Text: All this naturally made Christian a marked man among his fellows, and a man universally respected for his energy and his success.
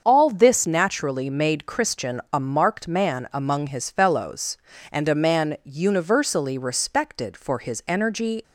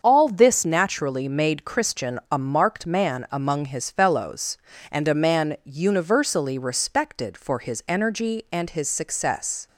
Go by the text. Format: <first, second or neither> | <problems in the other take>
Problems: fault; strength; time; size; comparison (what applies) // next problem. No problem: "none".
second | starts louder than the rest; until 1.0 s; 7 dB; also in the second // stops before "and his success"; at 8.4 s